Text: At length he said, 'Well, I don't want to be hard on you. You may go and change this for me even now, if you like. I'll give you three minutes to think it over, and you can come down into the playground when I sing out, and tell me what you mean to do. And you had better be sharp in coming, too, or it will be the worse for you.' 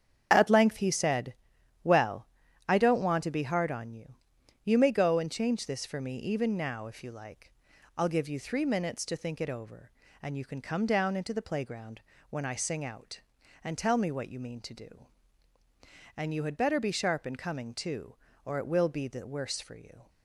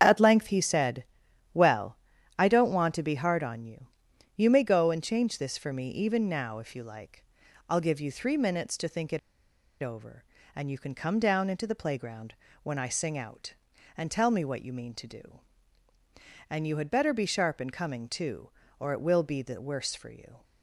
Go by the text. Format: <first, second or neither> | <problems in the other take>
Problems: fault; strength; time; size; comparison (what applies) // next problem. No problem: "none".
first | starts louder than the rest; strong; until 1.0 s; 8 dB; strong in the first // pauses between "it" and "over"; noticeable; at 9.1 s; 0.64 s long // pauses between "playground" and "when"; slight; at 12.3 s; 0.30 s long; slight in the first